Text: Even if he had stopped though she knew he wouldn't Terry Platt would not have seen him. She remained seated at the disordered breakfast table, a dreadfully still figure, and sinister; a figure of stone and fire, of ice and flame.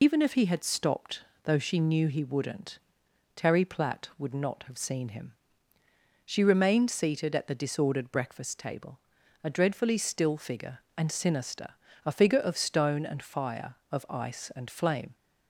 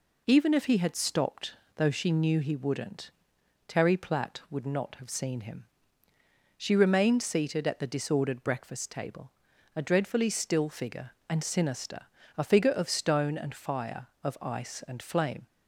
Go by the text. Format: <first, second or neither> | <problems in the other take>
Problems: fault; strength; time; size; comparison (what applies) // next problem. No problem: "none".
second | loses the start of "Even"; at 0.0 s; 70 ms // pauses between "stopped" and "though"; slight; at 1.2 s; 0.20 s long; slight in the second // pauses between "wouldn't" and "Terry"; noticeable; at 2.7 s; 0.56 s long; noticeable in the second